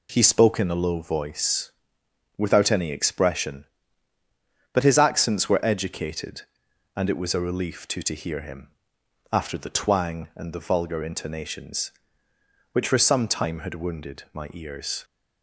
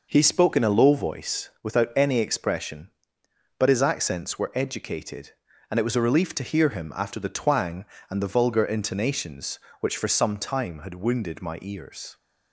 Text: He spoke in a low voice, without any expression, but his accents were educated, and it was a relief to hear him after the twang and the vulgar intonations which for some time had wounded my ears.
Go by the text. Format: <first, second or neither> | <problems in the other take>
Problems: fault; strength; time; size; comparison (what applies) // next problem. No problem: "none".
second | says "to" twice; at 8.0 s // pauses between "him" and "after"; noticeable; at 8.7 s; 0.62 s long